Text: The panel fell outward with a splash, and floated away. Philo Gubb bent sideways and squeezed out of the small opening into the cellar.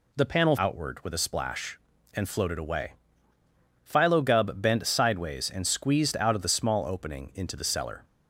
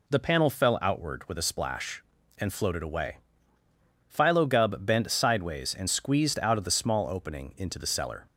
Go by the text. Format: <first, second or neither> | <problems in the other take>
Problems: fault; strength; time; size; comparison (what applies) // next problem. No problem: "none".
second | skips "fell"; at 0.5 s